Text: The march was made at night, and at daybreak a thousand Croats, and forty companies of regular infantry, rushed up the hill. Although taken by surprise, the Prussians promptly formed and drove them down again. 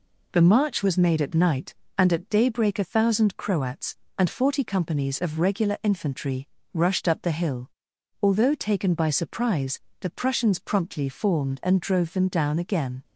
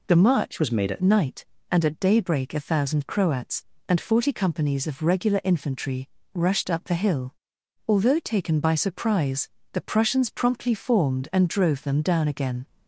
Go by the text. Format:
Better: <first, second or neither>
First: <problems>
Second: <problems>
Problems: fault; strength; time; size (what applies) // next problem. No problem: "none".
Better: first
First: none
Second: changes voice from "was" to "at"; from 0.5 to 1.0 s; 0.5 s long